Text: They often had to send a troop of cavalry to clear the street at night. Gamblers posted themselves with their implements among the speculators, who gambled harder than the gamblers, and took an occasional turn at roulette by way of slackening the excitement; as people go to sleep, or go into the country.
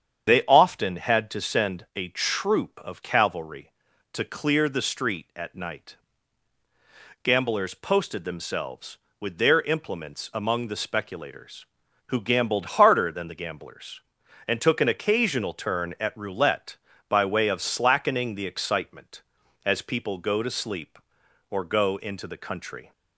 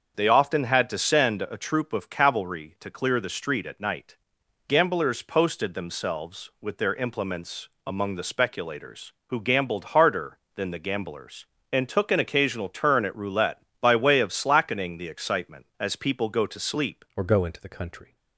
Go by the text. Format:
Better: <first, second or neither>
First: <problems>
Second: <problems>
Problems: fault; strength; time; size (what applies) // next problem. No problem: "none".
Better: first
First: starts louder than the rest; strong; until 1.3 s; 8 dB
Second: starts louder than the rest; strong; until 1.1 s; 7 dB // pauses between "implements" and "among"; slight; at 7.6 s; 0.18 s long // changes voice at "or"; from 17.1 s on; 1.0 s long